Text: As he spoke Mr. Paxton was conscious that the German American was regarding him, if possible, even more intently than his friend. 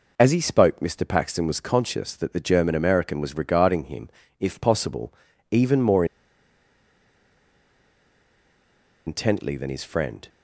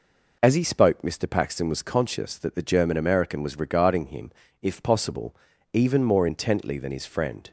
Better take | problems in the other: second | pauses between "more" and "intently"; strong; at 6.0 s; 3.0 s long

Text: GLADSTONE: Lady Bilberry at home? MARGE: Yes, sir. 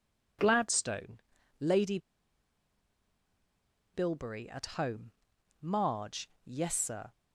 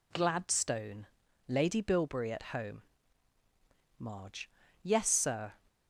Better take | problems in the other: second | pauses between "Lady" and "Bilberry"; strong; at 1.9 s; 1.9 s long

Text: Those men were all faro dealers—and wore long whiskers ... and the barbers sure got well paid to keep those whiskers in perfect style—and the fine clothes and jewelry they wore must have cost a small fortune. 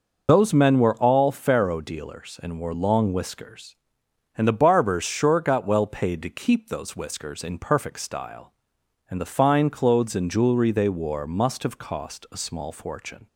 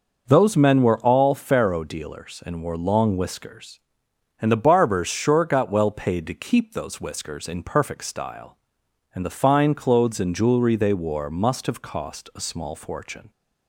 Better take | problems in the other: second | loses the start of "Those"; at 0.2 s; 45 ms

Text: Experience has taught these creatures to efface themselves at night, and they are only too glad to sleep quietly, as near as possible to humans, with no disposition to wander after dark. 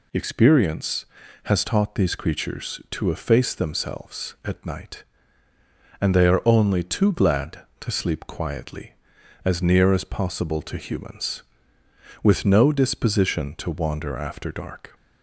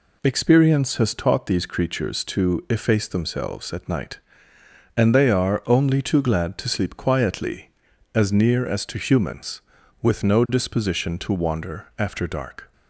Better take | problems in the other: first | skips "possible"; at 8.8 s

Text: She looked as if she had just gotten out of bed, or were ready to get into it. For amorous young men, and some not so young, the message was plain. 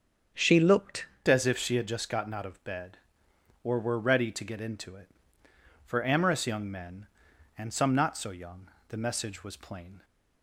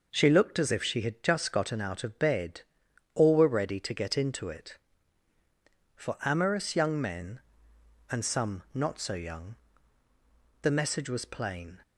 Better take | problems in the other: second | starts louder than the rest; until 1.6 s; 7 dB // changes voice at "as"; from 1.3 s on; 8.7 s long

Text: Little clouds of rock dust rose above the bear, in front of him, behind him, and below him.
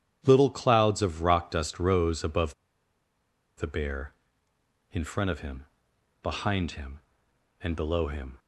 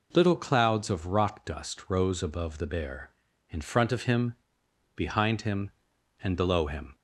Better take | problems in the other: second | starts louder than the rest; strong; until 1.2 s; 9.5 dB // pauses between "above" and "the"; at 2.5 s; 1.0 s long

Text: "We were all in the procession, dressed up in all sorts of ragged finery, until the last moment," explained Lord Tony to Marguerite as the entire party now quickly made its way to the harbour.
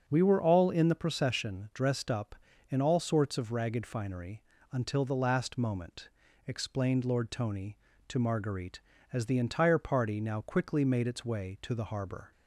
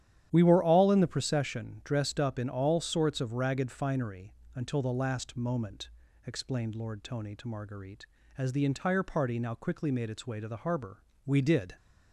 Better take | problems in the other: first | starts louder than the rest; strong; until 1.3 s; 10.5 dB; also in the first // goes on to say "We did"; from 11.2 s on; 0.50 s long

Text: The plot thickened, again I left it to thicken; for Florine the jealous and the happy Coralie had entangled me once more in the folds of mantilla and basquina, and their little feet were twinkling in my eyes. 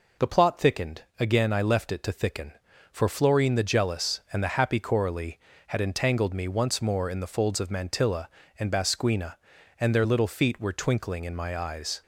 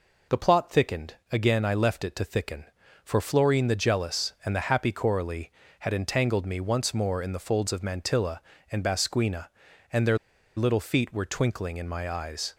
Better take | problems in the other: first | pauses between "their" and "little"; at 10.1 s; 0.39 s long

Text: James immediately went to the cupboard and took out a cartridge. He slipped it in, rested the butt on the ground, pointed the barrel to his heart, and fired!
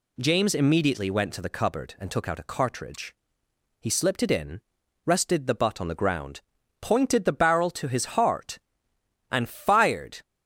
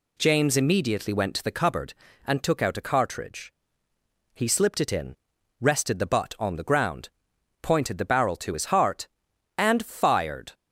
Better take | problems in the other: neither | none

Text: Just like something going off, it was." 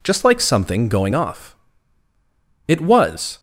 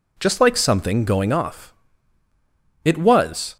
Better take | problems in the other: neither | none

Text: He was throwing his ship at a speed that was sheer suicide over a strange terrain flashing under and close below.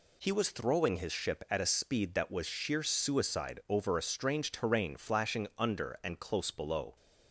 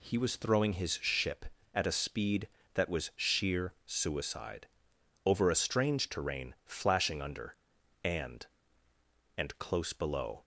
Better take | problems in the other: first | pauses between "suicide" and "over"; noticeable; at 4.6 s; 0.60 s long // says "and" twice; at 9.3 s

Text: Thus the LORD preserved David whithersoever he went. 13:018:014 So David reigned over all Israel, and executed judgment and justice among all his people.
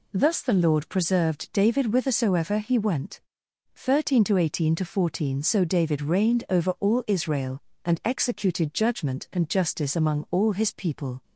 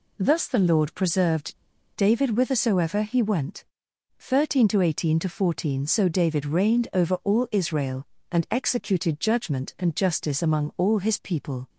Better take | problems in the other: first | pauses between "preserved" and "David"; at 1.5 s; 0.40 s long

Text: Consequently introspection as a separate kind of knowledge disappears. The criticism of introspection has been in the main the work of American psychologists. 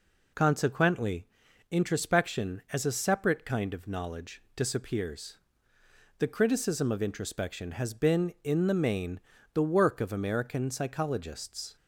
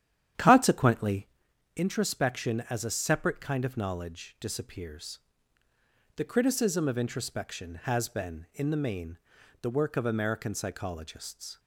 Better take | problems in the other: first | starts louder than the rest; strong; until 1.4 s; 10.5 dB // pauses between "Consequently" and "introspection"; noticeable; at 1.2 s; 0.48 s long; also in the first // pauses between "main" and "the"; at 9.1 s; 0.44 s long; slight in the first

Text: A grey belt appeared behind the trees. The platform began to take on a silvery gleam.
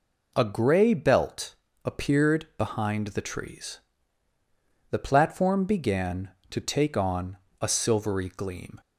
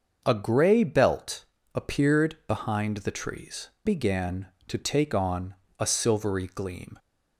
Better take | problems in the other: first | starts louder than the rest; until 1.2 s; 6.5 dB // pauses between "belt" and "appeared"; slight; at 1.4 s; 0.32 s long; slight in the first // skips "The platform"; at 3.7 s // pauses between "on" and "a"; slight; at 5.5 s; 0.24 s long; slight in the first

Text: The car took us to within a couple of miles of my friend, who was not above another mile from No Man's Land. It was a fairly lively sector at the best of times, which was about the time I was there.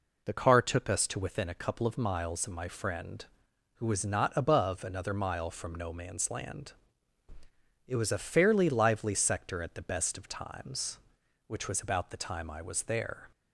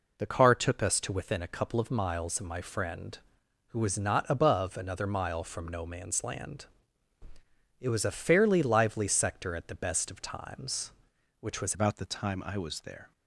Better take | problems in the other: first | changes voice at "about"; from 11.7 s on; 1.4 s long

